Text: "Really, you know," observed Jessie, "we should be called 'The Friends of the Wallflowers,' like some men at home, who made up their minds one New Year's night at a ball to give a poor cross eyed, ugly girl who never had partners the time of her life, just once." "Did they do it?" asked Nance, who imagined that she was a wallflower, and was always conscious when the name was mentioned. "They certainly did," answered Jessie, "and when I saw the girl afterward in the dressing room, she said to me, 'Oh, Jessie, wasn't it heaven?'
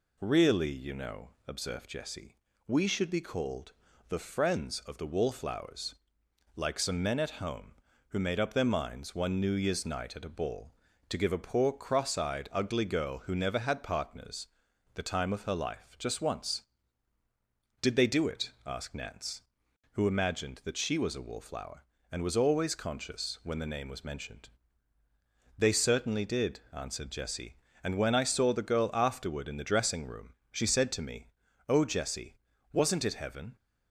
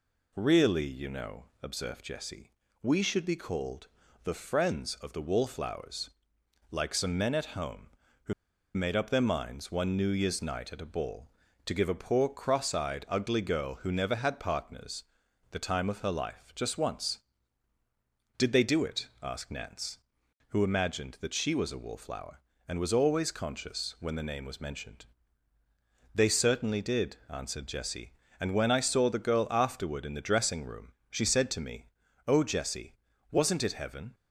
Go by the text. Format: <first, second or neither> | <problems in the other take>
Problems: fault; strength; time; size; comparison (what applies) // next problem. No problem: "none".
first | pauses between "called" and "The"; at 3.8 s; 0.38 s long; also in the first // pauses between "who" and "made"; at 8.3 s; 0.42 s long // pauses between "partners" and "the"; noticeable; at 15.0 s; 0.48 s long; noticeable in the first